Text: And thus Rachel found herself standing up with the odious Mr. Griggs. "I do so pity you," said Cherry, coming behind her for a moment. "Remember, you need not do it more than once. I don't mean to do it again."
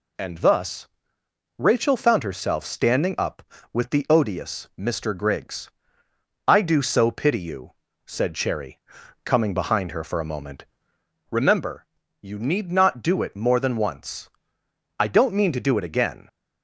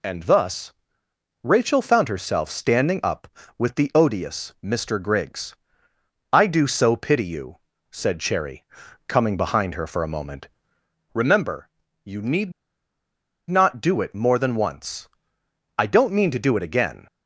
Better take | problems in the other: first | pauses between "thus" and "Rachel"; noticeable; at 0.7 s; 0.70 s long; noticeable in the first // pauses between "need" and "not"; at 12.5 s; 0.98 s long

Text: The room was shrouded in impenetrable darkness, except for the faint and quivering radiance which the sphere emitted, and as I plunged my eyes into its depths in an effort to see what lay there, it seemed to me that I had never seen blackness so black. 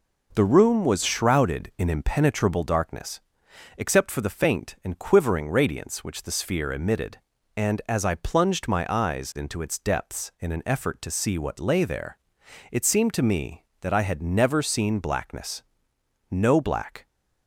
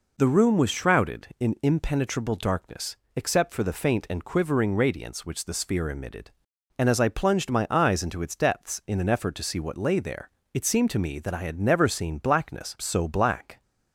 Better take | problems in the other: second | says "no" for "so"; at 16.3 s

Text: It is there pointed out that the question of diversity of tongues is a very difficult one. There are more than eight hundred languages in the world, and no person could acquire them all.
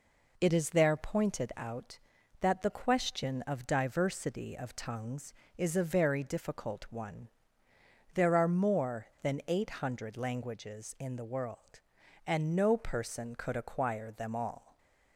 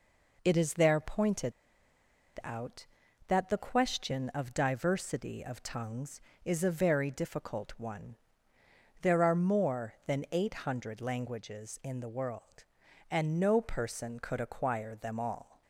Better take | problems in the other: first | pauses between "pointed" and "out"; noticeable; at 1.5 s; 0.91 s long

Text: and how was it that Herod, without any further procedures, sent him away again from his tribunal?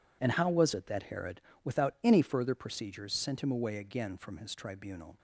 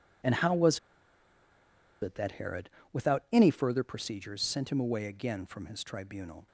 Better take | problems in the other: first | pauses between "was" and "it"; at 0.7 s; 1.2 s long

